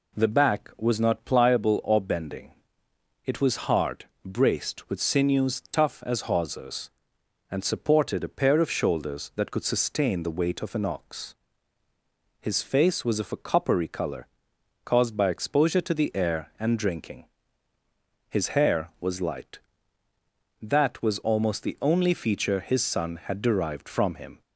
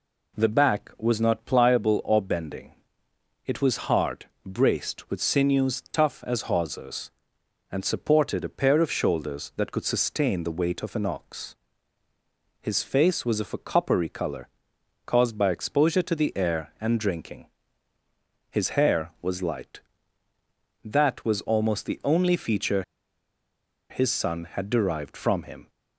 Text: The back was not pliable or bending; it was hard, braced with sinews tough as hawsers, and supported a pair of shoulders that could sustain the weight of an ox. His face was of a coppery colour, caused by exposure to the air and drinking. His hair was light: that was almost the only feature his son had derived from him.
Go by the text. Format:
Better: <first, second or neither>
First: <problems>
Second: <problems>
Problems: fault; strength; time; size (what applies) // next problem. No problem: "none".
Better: first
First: none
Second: pauses between "feature" and "his"; at 22.8 s; 1.0 s long